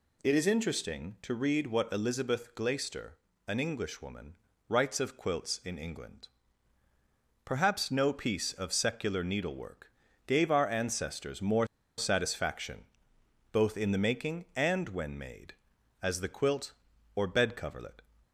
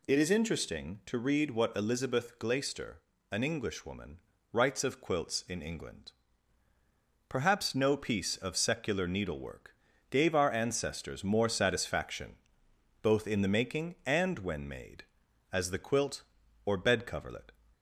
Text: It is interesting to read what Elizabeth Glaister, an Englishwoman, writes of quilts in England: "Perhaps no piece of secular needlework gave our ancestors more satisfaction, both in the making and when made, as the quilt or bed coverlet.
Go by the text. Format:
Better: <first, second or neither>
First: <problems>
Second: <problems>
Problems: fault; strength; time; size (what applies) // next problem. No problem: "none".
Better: second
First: pauses between "needlework" and "gave"; slight; at 9.9 s; 0.34 s long // pauses between "more" and "satisfaction"; slight; at 11.6 s; 0.31 s long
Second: pauses between "needlework" and "gave"; slight; at 9.7 s; 0.34 s long